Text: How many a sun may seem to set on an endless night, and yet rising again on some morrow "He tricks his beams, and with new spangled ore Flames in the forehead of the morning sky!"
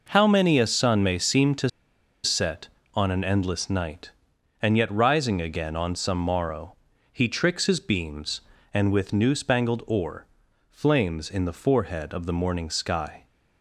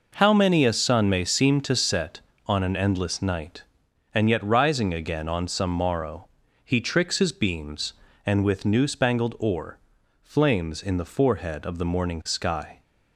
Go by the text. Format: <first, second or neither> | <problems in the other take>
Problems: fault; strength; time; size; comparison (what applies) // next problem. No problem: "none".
second | pauses between "to" and "set"; noticeable; at 1.6 s; 0.56 s long // pauses between "morrow" and "He"; slight; at 6.7 s; 0.36 s long; slight in the second // pauses between "ore" and "Flames"; at 10.2 s; 0.42 s long; also in the second